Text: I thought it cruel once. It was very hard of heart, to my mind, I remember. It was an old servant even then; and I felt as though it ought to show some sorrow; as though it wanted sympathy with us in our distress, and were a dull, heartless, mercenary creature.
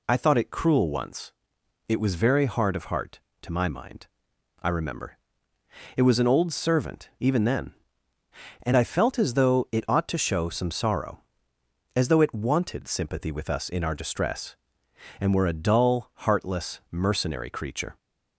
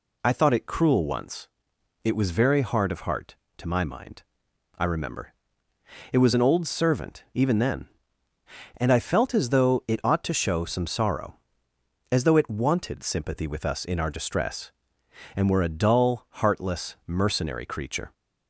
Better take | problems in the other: neither | none

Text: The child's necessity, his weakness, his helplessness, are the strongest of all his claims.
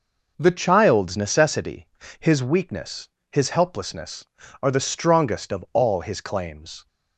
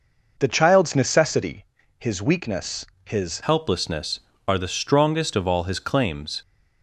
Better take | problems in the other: first | changes voice at "helplessness"; from 3.4 s on; 3.0 s long

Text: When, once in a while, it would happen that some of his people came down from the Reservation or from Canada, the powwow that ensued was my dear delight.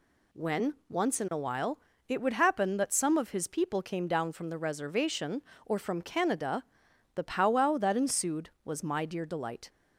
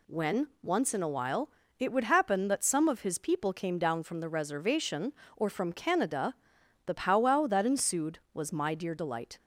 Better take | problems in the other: neither | none

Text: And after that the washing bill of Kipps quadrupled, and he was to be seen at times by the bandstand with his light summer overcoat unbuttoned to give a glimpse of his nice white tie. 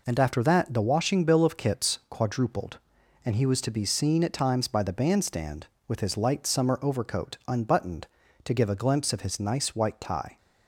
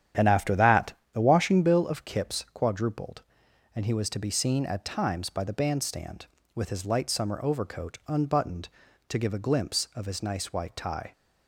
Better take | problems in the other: first | starts louder than the rest; strong; until 1.8 s; 9.5 dB // pauses between "that" and "the"; slight; at 0.9 s; 0.18 s long

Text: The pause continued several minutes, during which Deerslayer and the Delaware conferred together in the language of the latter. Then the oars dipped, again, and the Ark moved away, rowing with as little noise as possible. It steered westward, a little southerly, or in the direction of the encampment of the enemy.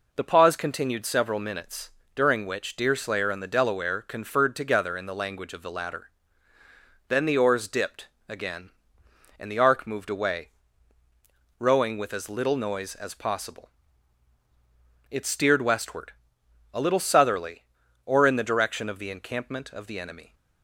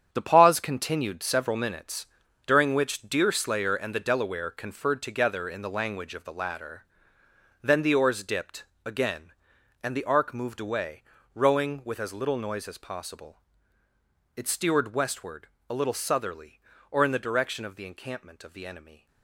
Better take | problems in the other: first | gets quieter; strong; throughout; 10 dB

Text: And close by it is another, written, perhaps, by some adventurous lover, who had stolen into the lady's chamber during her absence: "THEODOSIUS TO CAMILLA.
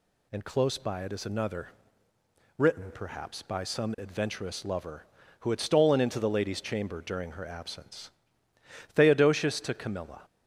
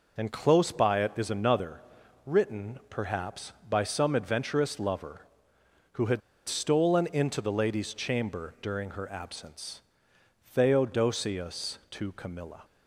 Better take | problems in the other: first | pauses between "had" and "stolen"; slight; at 6.2 s; 0.27 s long

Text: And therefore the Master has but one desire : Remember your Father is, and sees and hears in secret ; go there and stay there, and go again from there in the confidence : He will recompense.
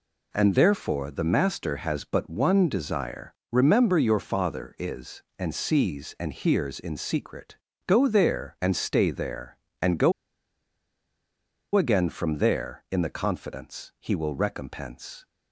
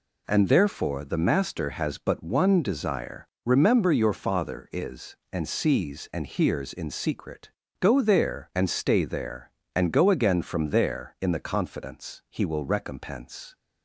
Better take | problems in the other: second | pauses between "go" and "again"; strong; at 10.1 s; 1.6 s long

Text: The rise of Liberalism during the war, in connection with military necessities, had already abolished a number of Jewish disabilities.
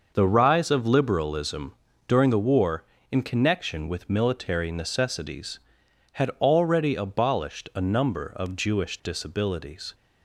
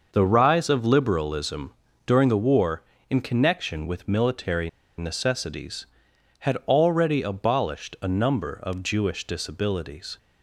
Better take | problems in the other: first | starts louder than the rest; noticeable; until 1.1 s; 6 dB; noticeable in the first // pauses between "Liberalism" and "during"; slight; at 1.7 s; 0.32 s long; slight in the first // pauses between "military" and "necessities"; slight; at 4.6 s; 0.28 s long

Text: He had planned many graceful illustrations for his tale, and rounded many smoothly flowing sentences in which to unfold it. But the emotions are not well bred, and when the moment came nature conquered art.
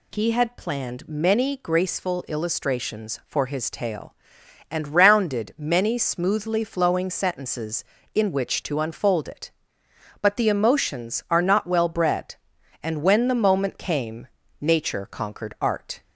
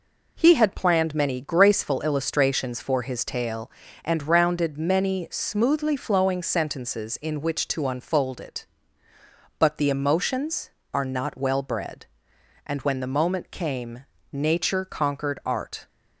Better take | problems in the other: neither | pauses between "came" and "nature"; slight; the same in both

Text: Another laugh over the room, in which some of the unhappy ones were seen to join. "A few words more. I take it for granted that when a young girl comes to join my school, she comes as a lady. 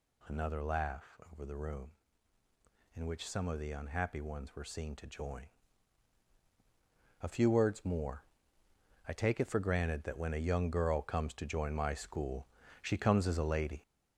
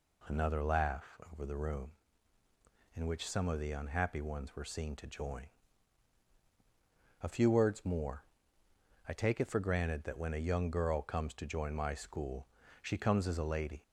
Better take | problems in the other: second | gets louder; noticeable; throughout; 5.5 dB // pauses between "laugh" and "over"; slight; at 1.1 s; 0.16 s long; slight in the second

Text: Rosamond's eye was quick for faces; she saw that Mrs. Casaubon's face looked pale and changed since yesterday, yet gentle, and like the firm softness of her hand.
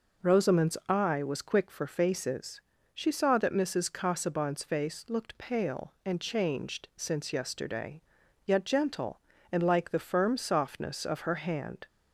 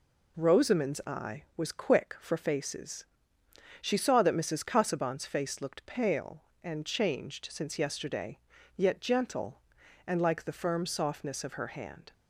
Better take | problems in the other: neither | none

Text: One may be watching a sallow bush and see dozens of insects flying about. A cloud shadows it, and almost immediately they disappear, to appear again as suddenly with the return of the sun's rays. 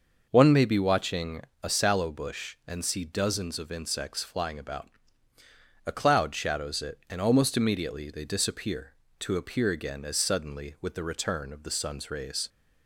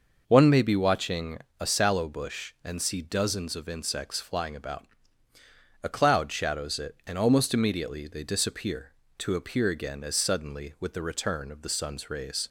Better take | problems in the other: neither | pauses between "watching" and "a"; slight; the same in both

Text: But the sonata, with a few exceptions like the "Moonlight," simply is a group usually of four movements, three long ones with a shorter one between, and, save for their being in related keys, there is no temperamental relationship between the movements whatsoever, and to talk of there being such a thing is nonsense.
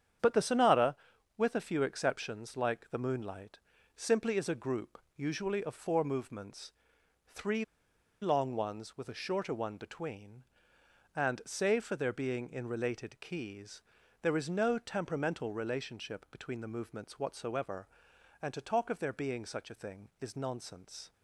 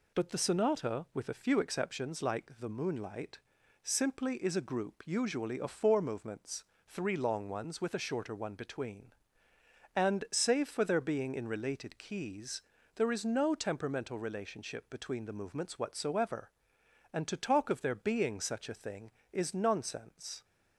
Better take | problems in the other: second | starts louder than the rest; strong; until 1.6 s; 8.5 dB // pauses between "group" and "usually"; slight; at 4.9 s; 0.18 s long // pauses between "three" and "long"; noticeable; at 7.6 s; 0.57 s long

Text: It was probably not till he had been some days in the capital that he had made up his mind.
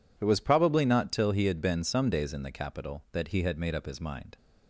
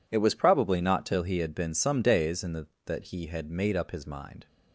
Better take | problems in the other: first | skips "capital"; at 2.7 s

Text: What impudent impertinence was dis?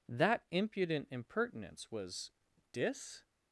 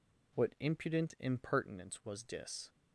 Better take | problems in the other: second | says "That" for "What"; at 0.0 s // pauses between "was" and "dis"; at 2.2 s; 0.42 s long

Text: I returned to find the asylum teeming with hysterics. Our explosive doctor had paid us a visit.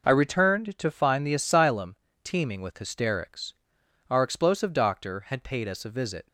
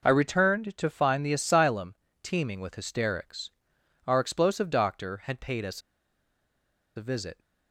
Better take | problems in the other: first | pauses between "asylum" and "teeming"; slight; at 1.9 s; 0.28 s long; slight in the first // pauses between "us" and "a"; at 5.8 s; 1.1 s long

